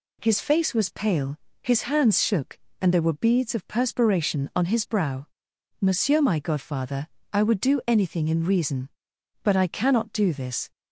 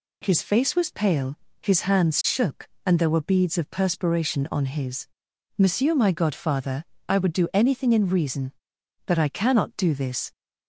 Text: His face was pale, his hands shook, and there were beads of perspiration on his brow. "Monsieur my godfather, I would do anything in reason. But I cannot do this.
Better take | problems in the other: first | skips "brow"; at 5.3 s

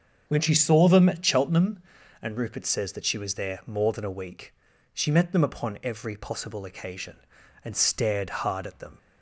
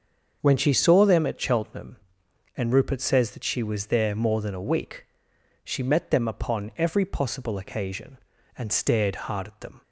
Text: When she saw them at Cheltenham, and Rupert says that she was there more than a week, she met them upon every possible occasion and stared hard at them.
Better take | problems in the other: neither | starts louder than the rest; the same in both

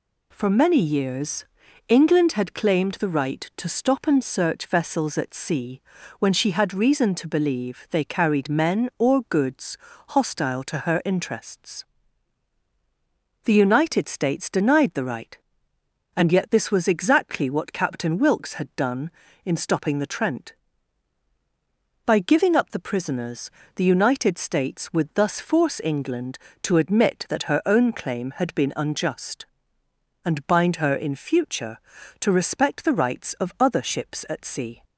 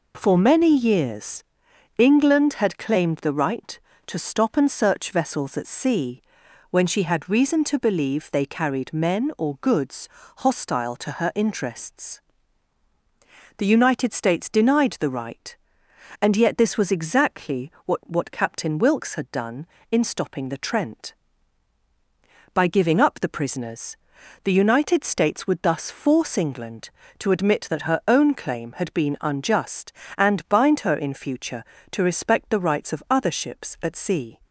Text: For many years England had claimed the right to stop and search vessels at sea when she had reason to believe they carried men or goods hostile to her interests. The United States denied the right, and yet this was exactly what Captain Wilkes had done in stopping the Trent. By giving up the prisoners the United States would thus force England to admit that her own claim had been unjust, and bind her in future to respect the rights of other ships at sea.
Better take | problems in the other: first | pauses between "years" and "England"; noticeable; at 1.4 s; 0.54 s long; also in the first // pauses between "sea" and "when"; noticeable; at 6.2 s; 0.48 s long; also in the first // pauses between "goods" and "hostile"; slight; at 10.0 s; 0.30 s long; slight in the first // says "what" twice; at 18.0 s // pauses between "prisoners" and "the"; noticeable; at 23.9 s; 0.46 s long; slight in the first

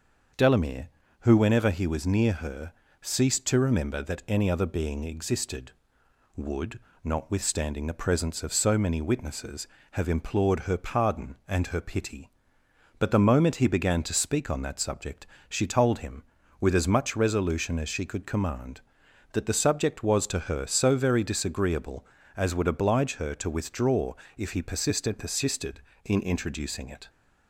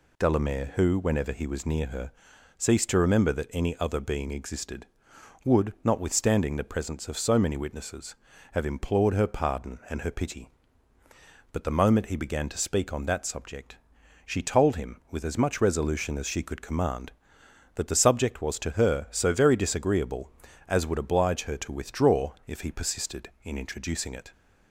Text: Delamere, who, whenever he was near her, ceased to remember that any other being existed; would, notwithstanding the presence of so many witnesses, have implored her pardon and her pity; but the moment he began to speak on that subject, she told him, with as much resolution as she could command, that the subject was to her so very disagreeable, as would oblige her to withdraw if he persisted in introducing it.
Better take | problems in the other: second | starts louder than the rest; until 1.6 s; 6.5 dB // pauses between "withdraw" and "if"; slight; at 24.1 s; 0.24 s long // says "persisted" twice; at 25.1 s

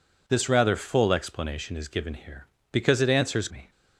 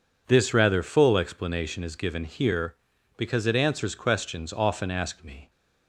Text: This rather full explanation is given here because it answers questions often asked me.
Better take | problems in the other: second | skips "questions often asked"; at 3.4 s

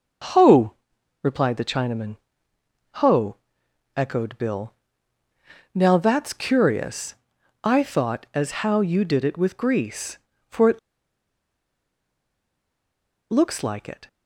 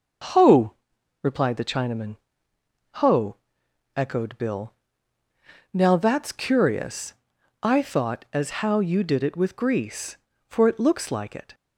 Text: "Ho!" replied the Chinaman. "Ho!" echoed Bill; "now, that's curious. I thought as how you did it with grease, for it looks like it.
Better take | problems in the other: second | starts louder than the rest; until 1.8 s; 6 dB; noticeable in the second // pauses between "it" and "looks"; strong; at 10.7 s; 2.5 s long

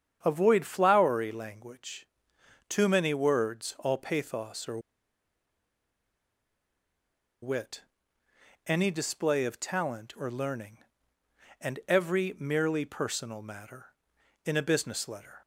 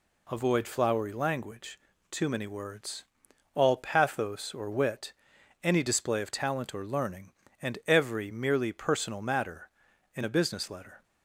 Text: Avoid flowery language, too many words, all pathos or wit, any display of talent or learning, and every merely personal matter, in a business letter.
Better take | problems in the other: second | starts louder than the rest; strong; until 1.2 s; 8 dB // pauses between "or" and "wit"; strong; at 4.7 s; 2.6 s long

